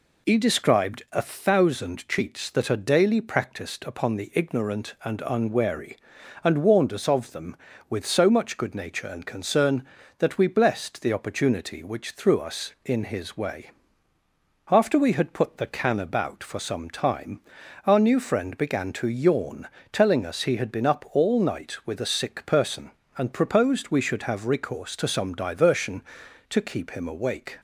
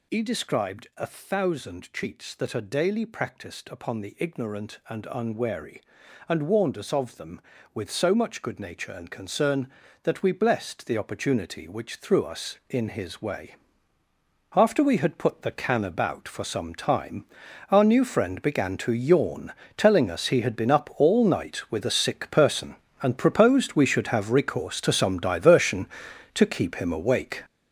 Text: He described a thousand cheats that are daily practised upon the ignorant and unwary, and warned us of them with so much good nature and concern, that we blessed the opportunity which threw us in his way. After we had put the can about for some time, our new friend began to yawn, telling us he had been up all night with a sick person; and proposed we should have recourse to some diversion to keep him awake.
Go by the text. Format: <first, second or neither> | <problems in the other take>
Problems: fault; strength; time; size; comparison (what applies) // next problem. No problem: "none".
first | gets louder; strong; throughout; 10.5 dB